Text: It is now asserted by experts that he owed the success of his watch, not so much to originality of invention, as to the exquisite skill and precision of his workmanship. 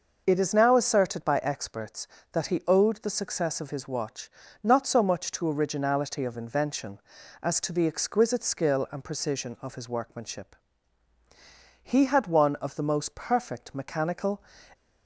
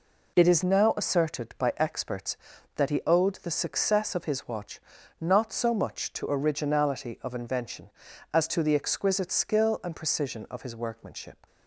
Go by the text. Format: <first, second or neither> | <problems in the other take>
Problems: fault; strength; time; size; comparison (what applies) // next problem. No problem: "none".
second | goes on to say "He had one of the most perfect mechanical"; strong; from 11.8 s on; 2.6 s long